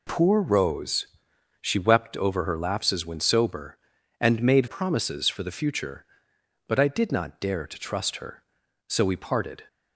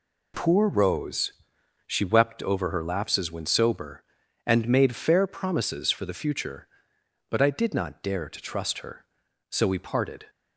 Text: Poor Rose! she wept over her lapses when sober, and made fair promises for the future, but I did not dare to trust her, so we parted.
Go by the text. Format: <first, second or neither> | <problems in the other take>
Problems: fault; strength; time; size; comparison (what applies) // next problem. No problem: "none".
second | skips "fair"; at 4.6 s